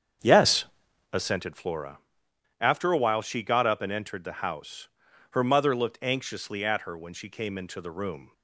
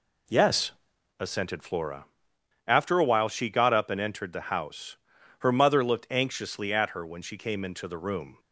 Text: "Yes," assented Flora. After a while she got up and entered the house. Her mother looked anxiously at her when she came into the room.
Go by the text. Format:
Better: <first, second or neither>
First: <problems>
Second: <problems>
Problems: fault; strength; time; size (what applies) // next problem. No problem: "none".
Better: second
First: starts louder than the rest; strong; until 1.5 s; 7.5 dB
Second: none